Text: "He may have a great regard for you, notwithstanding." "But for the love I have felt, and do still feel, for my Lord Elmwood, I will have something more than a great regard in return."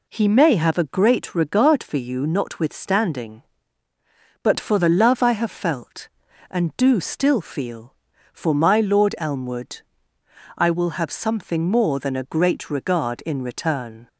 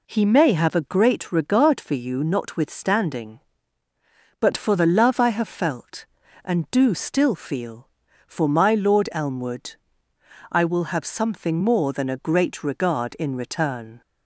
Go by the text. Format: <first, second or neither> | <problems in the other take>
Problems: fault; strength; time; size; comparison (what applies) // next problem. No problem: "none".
neither | none